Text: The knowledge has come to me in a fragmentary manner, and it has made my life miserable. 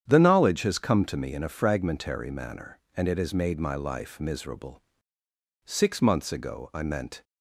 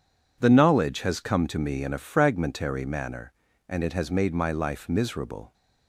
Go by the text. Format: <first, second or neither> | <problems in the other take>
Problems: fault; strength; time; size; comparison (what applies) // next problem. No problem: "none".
second | starts louder than the rest; strong; until 1.1 s; 9 dB // goes on to say "Six months ago I meant"; from 5.6 s on; 1.5 s long